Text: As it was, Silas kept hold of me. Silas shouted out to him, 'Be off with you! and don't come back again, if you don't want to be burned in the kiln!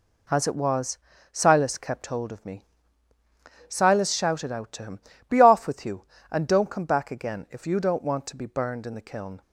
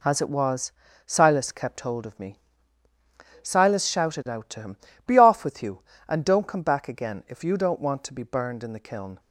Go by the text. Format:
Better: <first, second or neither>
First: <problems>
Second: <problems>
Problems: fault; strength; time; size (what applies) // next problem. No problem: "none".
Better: neither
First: none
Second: none